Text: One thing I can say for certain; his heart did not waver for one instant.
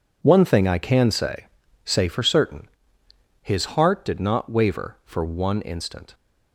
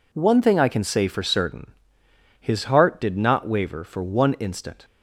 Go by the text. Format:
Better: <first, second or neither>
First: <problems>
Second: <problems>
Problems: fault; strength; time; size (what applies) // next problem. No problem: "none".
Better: second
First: says "say" twice; at 1.8 s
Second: none